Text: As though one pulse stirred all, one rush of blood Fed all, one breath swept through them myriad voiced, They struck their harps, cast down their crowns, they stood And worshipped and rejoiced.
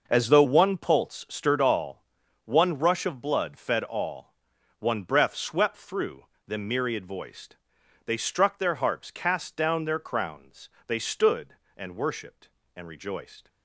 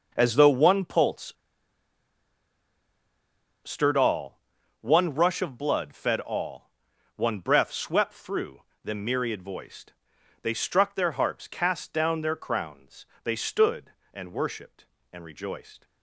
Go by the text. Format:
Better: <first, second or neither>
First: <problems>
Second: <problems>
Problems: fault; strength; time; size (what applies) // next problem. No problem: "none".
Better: first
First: pauses between "through" and "them"; slight; at 6.2 s; 0.20 s long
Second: pauses between "pulse" and "stirred"; strong; at 1.3 s; 2.3 s long // pauses between "through" and "them"; slight; at 8.6 s; 0.20 s long